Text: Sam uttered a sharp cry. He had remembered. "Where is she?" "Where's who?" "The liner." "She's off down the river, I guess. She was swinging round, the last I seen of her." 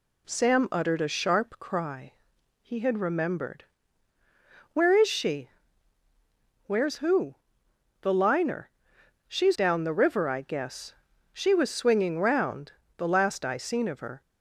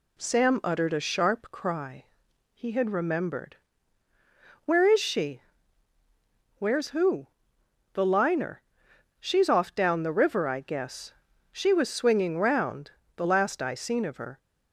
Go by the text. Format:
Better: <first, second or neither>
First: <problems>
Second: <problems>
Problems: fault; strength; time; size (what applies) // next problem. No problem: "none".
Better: second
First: skips "off"; at 9.5 s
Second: none